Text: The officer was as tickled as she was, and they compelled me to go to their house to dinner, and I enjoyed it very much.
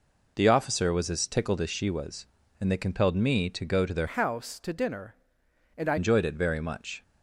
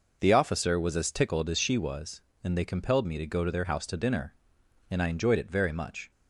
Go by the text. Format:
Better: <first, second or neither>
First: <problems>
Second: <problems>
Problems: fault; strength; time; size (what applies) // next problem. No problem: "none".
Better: second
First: changes voice from "house" to "I"; from 4.0 to 5.9 s; 1.9 s long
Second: none